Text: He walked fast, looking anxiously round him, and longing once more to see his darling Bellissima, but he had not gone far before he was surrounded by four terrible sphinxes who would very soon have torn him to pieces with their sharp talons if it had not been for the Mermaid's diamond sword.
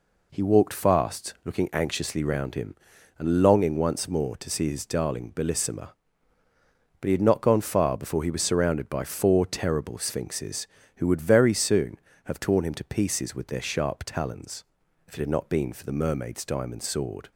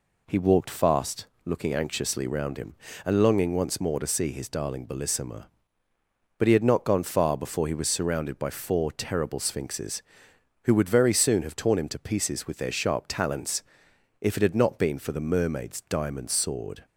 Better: neither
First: pauses between "talons" and "if"; noticeable; at 14.6 s; 0.46 s long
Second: pauses between "talons" and "if"; noticeable; at 13.6 s; 0.56 s long

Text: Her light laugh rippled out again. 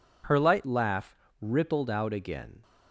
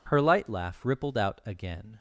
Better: second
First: changes voice at "laugh"; from 0.6 s on; 2.0 s long // pauses between "laugh" and "rippled"; slight; at 1.1 s; 0.26 s long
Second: none

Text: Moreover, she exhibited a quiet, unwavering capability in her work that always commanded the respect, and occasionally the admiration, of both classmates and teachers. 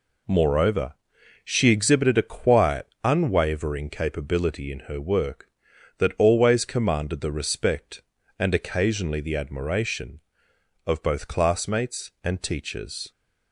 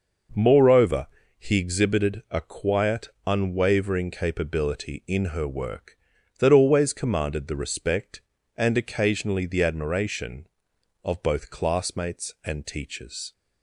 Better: first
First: none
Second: says "he" for "she"; at 1.3 s

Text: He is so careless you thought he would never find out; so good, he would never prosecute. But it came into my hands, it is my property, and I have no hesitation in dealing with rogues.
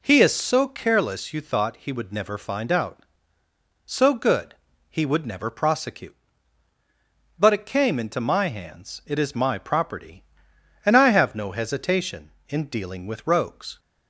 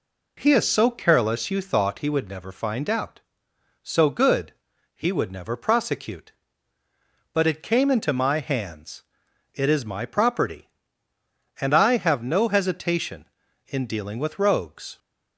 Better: neither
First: none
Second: none

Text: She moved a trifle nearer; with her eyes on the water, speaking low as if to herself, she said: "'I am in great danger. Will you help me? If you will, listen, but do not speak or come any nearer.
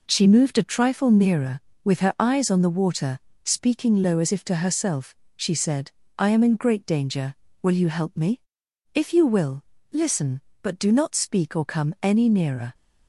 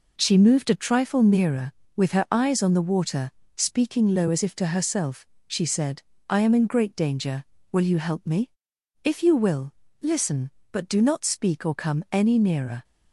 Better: neither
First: none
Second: none

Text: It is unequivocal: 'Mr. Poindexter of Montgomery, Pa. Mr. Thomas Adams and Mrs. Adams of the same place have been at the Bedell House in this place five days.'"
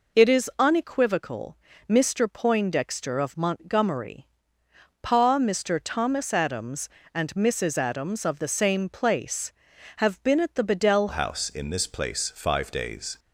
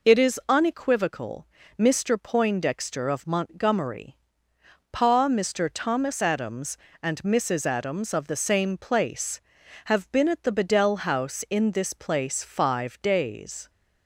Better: second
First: changes voice at "House"; from 11.1 s on; 2.0 s long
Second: none

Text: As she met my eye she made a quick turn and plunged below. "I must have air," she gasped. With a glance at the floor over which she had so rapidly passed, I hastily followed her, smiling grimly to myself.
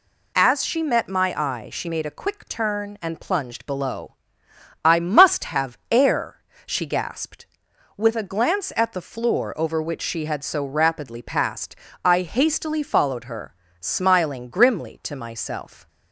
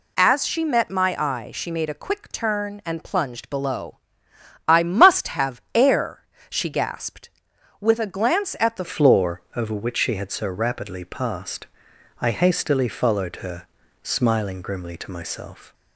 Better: first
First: none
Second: changes voice at "floor"; from 8.8 s on; 6.9 s long

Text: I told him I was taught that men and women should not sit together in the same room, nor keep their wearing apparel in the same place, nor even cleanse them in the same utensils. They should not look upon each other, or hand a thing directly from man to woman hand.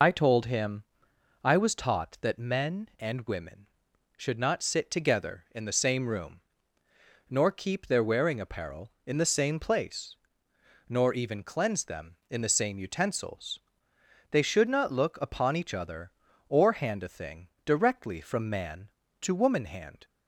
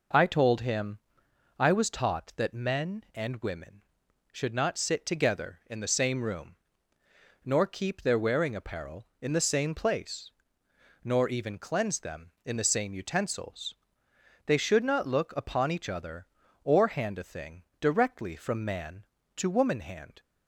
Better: second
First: loses the start of "I"; at 0.0 s; 55 ms // pauses between "him" and "I"; noticeable; at 0.8 s; 0.60 s long // pauses between "thing" and "directly"; slight; at 17.4 s; 0.16 s long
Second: pauses between "him" and "I"; noticeable; at 0.9 s; 0.60 s long // pauses between "thing" and "directly"; slight; at 17.6 s; 0.16 s long

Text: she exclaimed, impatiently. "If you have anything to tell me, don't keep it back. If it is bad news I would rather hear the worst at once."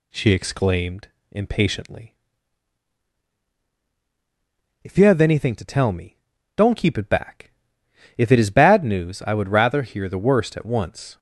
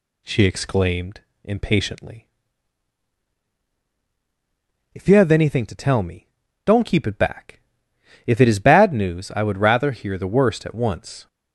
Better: neither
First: none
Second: none

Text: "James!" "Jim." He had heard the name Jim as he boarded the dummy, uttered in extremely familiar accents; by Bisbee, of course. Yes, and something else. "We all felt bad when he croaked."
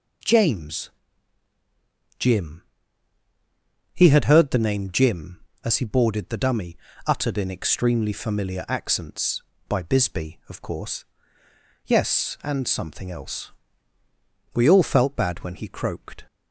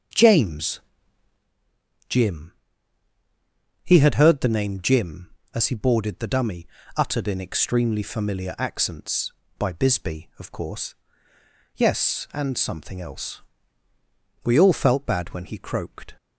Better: first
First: none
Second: starts louder than the rest; until 1.5 s; 6.5 dB

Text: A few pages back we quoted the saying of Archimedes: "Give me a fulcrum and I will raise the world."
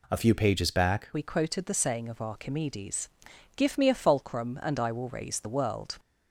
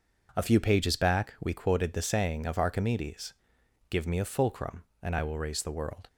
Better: second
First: changes voice at "we"; from 1.1 s on; 4.8 s long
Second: none

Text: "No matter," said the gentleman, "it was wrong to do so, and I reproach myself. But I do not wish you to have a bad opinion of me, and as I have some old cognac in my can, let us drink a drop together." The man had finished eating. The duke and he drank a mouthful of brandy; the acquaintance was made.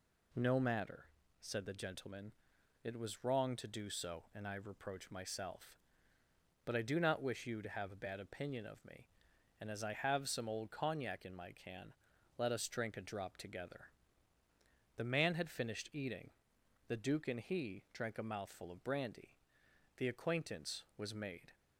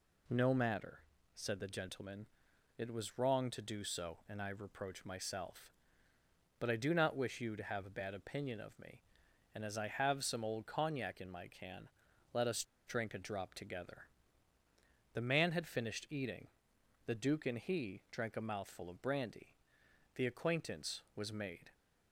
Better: first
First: none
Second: pauses between "us" and "drink"; slight; at 12.6 s; 0.24 s long

